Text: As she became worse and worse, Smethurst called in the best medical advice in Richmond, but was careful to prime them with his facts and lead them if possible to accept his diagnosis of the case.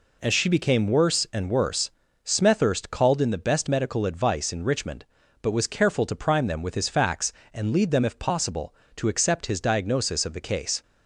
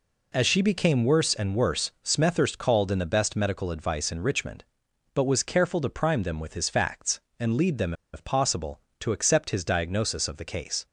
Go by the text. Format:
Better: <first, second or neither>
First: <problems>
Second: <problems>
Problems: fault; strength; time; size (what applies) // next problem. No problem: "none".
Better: first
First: none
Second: pauses between "them" and "if"; slight; at 7.9 s; 0.20 s long